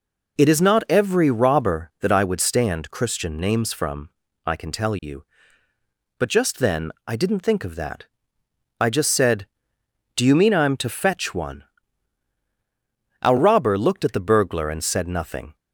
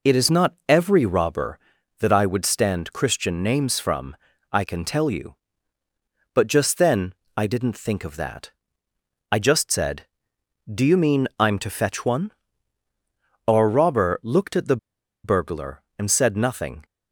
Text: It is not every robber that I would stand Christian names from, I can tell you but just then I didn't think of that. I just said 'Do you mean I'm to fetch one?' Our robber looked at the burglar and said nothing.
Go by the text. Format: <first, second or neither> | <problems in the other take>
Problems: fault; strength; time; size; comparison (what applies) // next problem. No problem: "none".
first | pauses between "then" and "I"; slight; at 7.1 s; 0.22 s long // pauses between "the" and "burglar"; noticeable; at 14.7 s; 0.47 s long